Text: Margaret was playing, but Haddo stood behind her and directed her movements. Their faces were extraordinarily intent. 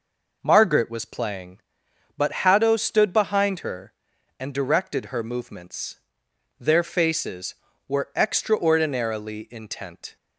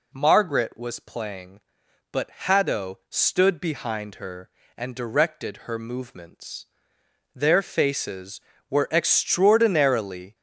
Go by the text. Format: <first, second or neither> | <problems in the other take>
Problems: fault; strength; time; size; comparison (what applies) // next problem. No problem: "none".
first | stops before "intent"; at 10.3 s